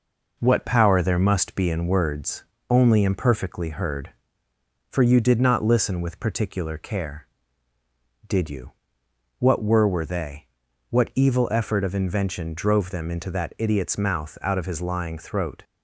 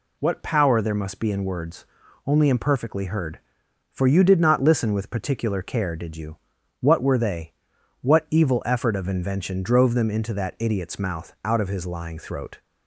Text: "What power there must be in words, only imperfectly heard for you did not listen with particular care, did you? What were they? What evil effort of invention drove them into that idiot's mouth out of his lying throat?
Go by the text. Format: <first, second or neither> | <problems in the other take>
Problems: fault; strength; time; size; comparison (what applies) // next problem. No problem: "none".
second | says "were" twice; at 9.8 s